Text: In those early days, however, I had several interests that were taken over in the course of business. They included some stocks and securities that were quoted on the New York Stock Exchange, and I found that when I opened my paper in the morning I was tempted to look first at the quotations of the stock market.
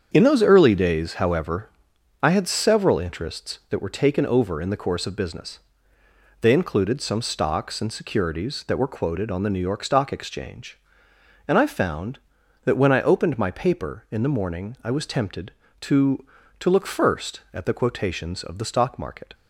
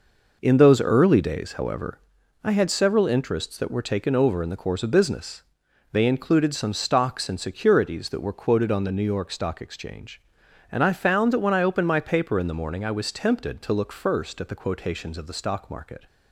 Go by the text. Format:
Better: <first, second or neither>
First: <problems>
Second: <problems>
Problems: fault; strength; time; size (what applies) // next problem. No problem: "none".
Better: second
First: starts louder than the rest; strong; until 1.1 s; 7.5 dB // says "to" twice; at 16.5 s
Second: none